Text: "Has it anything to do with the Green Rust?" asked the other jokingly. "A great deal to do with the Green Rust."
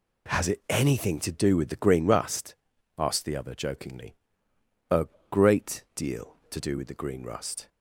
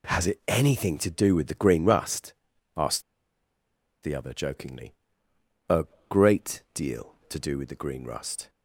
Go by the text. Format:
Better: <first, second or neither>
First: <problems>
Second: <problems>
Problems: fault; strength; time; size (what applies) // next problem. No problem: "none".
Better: first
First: pauses between "A" and "great"; slight; at 5.0 s; 0.24 s long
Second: pauses between "asked" and "the"; at 3.0 s; 1.0 s long // pauses between "A" and "great"; slight; at 5.8 s; 0.24 s long